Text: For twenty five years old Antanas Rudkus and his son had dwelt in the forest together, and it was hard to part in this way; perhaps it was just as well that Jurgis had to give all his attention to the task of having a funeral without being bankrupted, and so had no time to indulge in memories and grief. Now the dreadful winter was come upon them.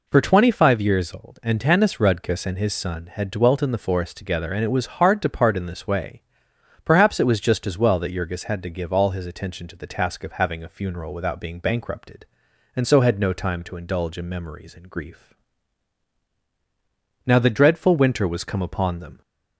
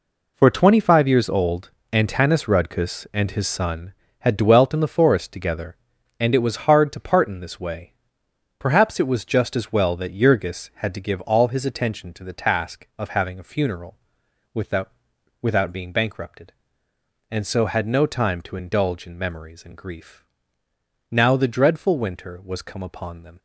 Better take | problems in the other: first | pauses between "old" and "Antanas"; slight; at 1.7 s; 0.22 s long // pauses between "funeral" and "without"; noticeable; at 13.9 s; 0.58 s long // says "without" twice; at 15.4 s

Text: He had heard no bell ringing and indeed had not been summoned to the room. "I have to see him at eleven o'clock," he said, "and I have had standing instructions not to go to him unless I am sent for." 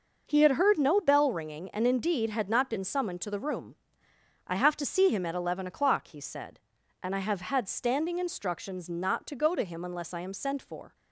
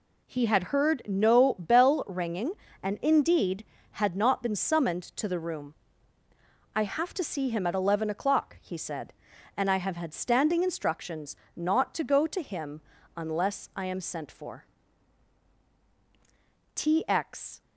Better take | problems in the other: first | pauses between "instructions" and "not"; slight; at 11.3 s; 0.22 s long // pauses between "him" and "unless"; at 12.7 s; 0.38 s long // goes on to say "T X"; noticeable; from 16.7 s on; 0.88 s long

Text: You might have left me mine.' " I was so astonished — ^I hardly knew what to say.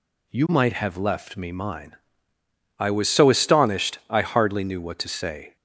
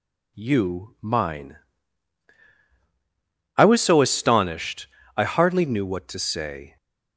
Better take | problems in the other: first | skips "might have left me"; at 0.9 s

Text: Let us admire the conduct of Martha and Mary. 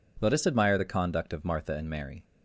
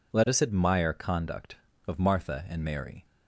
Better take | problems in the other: first | skips "the"; at 0.9 s

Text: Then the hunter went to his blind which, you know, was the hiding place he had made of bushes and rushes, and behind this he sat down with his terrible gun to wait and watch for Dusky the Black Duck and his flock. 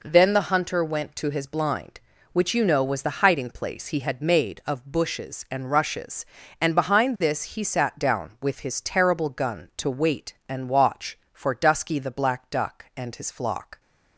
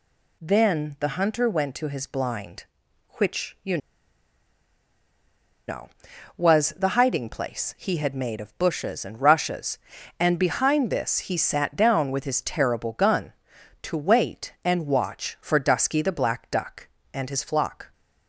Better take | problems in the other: first | pauses between "you" and "know"; strong; at 3.7 s; 1.8 s long

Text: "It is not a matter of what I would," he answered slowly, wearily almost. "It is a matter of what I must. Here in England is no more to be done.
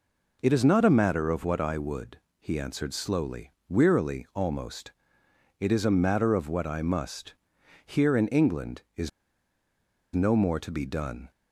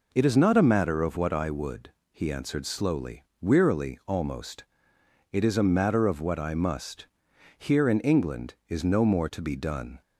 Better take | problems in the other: second | pauses between "is" and "no"; at 9.0 s; 1.0 s long

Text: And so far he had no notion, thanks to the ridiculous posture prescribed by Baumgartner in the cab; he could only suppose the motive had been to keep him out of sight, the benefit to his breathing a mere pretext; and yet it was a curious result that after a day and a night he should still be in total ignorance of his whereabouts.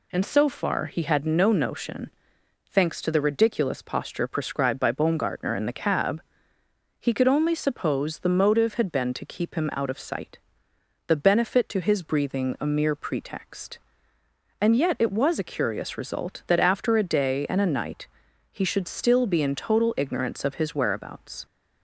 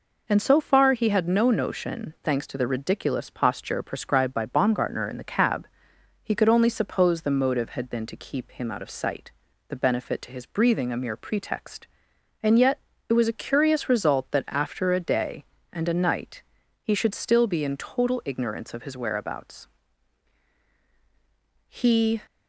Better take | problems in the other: first | pauses between "yet" and "it"; slight; at 12.7 s; 0.30 s long // pauses between "night" and "he"; at 16.4 s; 0.40 s long; also in the first // goes on to say "He"; from 21.6 s on; 0.54 s long

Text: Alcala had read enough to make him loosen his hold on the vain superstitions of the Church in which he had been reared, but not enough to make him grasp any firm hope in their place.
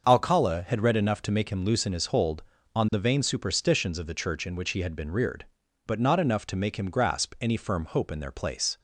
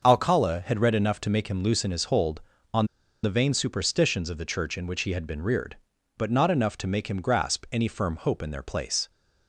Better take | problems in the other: first | starts louder than the rest; until 1.1 s; 6.5 dB; also in the first // pauses between "on" and "the"; at 2.8 s; 0.36 s long

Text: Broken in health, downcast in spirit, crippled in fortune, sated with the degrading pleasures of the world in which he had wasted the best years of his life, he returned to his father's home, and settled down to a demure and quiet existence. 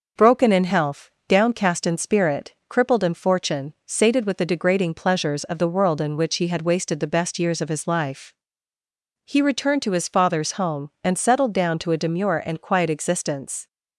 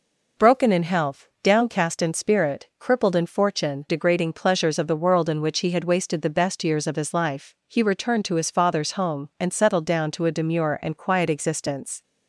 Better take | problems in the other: first | skips "sated with the"; at 3.8 s

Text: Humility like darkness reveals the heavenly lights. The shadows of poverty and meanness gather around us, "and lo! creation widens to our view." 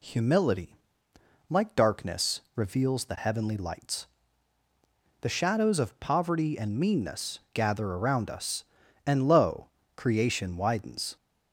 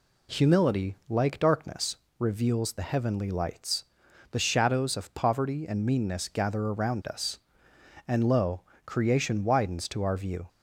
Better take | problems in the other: second | pauses between "Humility" and "like"; noticeable; at 0.7 s; 0.74 s long // pauses between "darkness" and "reveals"; slight; at 2.4 s; 0.16 s long; slight in the second // stops before "to our view"; at 11.1 s

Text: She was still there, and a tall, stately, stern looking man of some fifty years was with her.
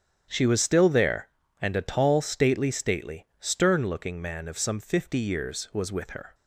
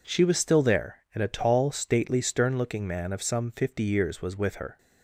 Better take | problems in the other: second | starts louder than the rest; strong; until 1.3 s; 9 dB // says "stately" twice; at 2.7 s

